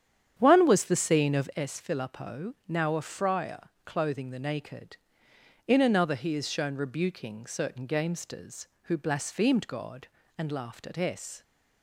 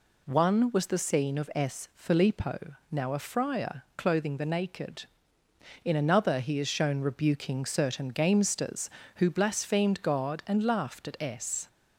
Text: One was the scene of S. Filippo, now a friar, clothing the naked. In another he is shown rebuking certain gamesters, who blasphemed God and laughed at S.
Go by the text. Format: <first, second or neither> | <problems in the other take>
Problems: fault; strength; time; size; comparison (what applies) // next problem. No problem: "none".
second | starts louder than the rest; strong; until 1.7 s; 9 dB